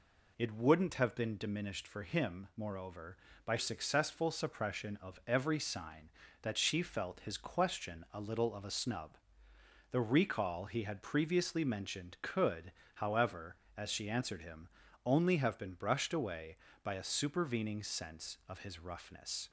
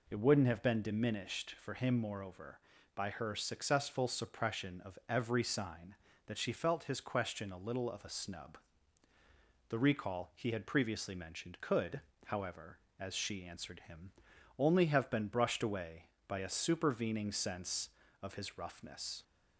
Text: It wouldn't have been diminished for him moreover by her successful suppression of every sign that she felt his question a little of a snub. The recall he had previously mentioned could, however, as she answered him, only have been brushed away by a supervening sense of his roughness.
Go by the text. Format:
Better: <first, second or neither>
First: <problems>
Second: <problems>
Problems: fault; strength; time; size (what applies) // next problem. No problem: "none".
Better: second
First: skips "her"; at 3.5 s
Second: none